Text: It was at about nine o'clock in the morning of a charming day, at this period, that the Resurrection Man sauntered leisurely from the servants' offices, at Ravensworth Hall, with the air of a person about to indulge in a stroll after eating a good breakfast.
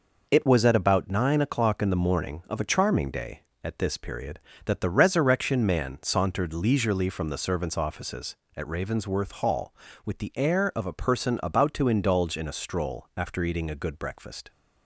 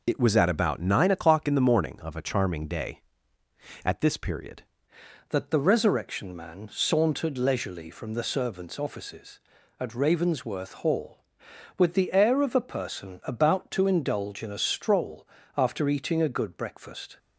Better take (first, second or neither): first